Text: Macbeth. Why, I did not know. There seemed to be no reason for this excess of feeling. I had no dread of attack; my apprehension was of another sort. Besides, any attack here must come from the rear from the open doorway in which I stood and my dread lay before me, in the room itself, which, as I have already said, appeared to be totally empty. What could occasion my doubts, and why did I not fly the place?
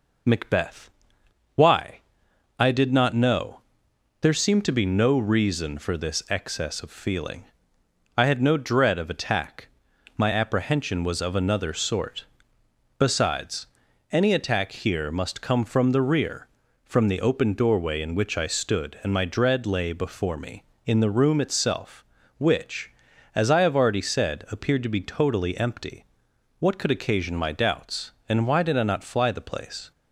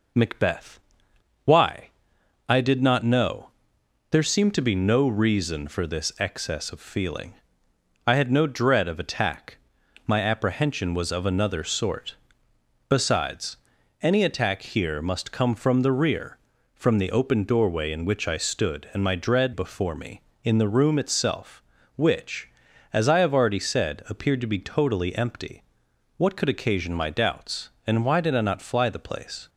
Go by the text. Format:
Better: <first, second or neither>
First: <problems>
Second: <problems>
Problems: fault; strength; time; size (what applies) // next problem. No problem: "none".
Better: first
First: none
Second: skips "lay"; at 19.5 s